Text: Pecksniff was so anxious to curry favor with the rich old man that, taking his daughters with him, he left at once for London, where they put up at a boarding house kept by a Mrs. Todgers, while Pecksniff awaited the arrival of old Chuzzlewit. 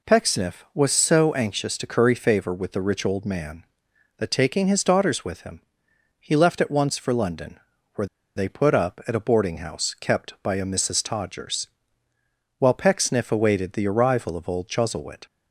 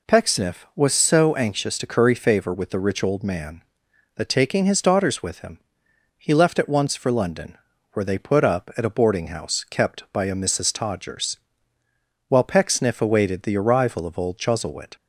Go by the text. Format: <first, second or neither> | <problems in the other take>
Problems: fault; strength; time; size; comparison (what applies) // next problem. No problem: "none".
second | pauses between "where" and "they"; slight; at 8.0 s; 0.29 s long